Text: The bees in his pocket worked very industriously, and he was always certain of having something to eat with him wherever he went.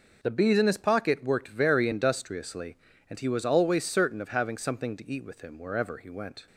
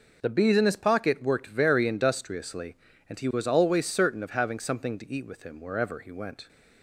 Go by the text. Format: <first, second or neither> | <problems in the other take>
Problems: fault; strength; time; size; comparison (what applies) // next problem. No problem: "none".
neither | none